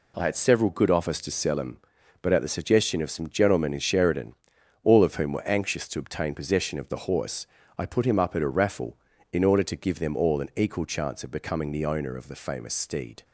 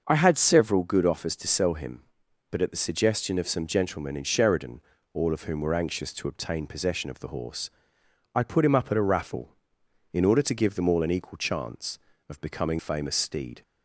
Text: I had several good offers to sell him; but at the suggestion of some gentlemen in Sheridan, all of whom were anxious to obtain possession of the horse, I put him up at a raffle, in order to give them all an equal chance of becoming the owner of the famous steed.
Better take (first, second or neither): first